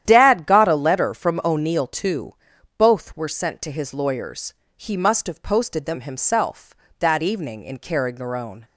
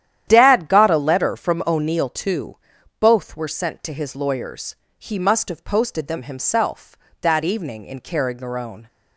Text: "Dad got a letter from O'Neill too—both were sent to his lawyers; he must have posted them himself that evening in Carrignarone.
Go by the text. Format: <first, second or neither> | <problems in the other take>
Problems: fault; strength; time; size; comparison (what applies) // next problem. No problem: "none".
neither | starts louder than the rest; strong; the same in both